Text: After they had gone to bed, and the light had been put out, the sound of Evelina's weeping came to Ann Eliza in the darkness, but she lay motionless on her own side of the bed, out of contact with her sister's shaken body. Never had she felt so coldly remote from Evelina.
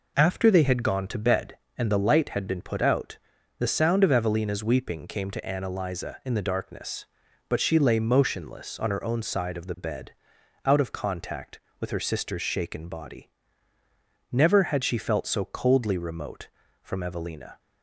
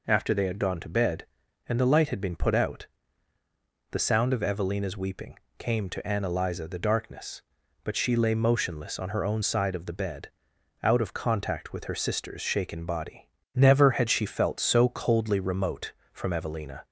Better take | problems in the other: first | pauses between "weeping" and "came"; slight; at 5.3 s; 0.20 s long // skips "in"; at 6.6 s

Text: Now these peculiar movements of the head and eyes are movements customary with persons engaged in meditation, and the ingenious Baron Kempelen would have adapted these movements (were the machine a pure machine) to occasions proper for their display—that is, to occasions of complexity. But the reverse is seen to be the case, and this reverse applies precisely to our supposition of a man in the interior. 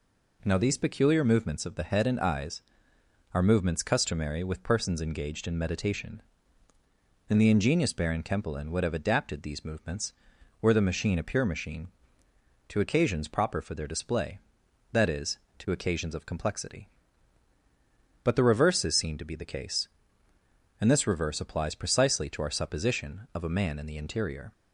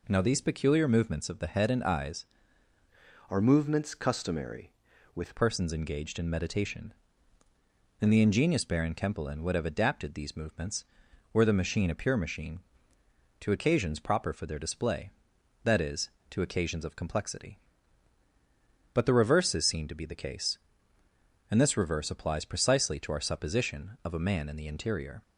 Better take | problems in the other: first | changes voice from "are" to "with"; from 3.2 to 5.3 s; 2.1 s long

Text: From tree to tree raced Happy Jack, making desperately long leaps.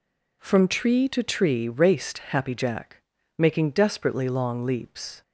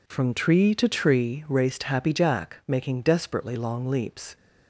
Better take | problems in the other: neither | none

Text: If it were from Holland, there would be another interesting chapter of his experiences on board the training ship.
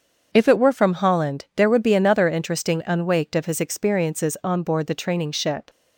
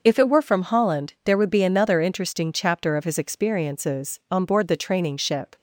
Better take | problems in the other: second | starts louder than the rest; until 1.3 s; 7 dB // says "unwaked" for "chapter"; at 2.8 s

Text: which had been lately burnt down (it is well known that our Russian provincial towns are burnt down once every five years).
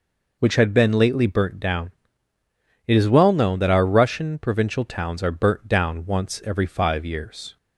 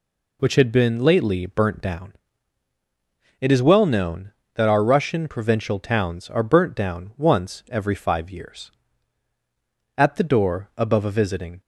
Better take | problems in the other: first | goes on to say "At the door above a visiting"; from 9.9 s on; 1.6 s long

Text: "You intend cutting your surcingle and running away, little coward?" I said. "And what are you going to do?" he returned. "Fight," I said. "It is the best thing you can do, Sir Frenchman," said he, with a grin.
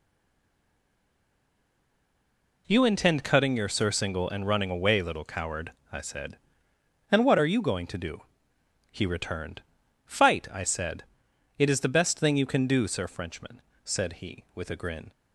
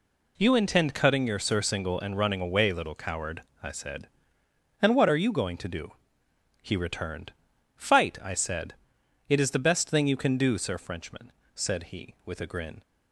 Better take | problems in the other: second | stays silent before the first word; strong; until 2.6 s; 2.6 s long

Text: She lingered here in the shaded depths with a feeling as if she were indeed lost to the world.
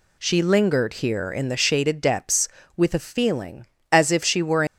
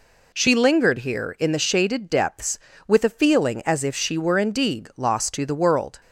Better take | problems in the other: second | stops before "indeed lost to the world"; at 4.6 s

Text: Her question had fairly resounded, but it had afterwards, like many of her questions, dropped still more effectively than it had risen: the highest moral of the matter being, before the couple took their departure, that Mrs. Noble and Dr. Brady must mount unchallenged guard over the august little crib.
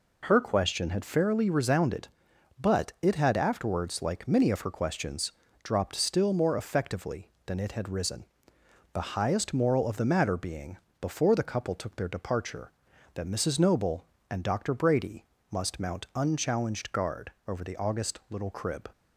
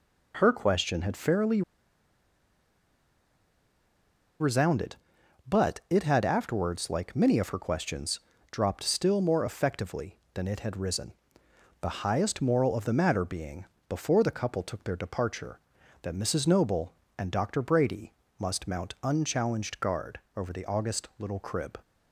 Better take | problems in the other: first | pauses between "fairly" and "resounded"; strong; at 1.6 s; 2.7 s long // pauses between "Brady" and "must"; slight; at 18.1 s; 0.26 s long; slight in the first

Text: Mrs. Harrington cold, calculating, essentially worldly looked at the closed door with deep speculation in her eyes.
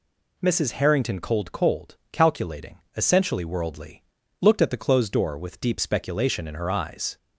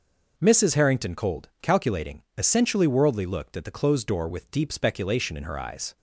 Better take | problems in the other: second | says "cold" twice; at 1.5 s // pauses between "worldly" and "looked"; slight; at 4.0 s; 0.36 s long

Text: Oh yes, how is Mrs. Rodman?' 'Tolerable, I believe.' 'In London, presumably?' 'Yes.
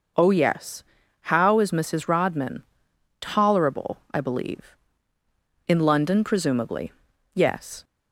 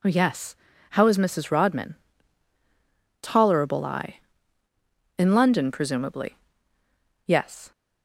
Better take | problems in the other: first | skips "believe"; at 4.6 s

